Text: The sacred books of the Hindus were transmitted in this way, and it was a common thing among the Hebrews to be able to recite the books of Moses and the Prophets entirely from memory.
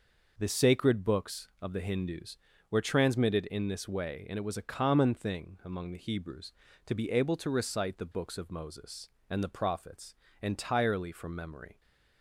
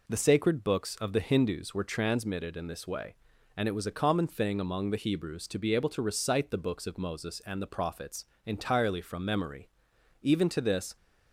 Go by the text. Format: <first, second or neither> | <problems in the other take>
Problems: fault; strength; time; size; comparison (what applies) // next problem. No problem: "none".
first | pauses between "Prophets" and "entirely"; slight; at 8.2 s; 0.18 s long; slight in the first // goes on to say "Even to this"; noticeable; from 10.2 s on; 0.73 s long